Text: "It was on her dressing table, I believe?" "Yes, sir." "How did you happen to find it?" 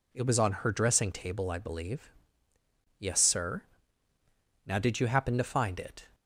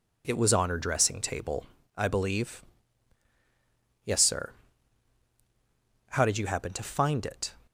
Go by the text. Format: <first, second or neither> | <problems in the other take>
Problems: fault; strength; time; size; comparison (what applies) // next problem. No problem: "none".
second | says "Now" for "How"; at 4.6 s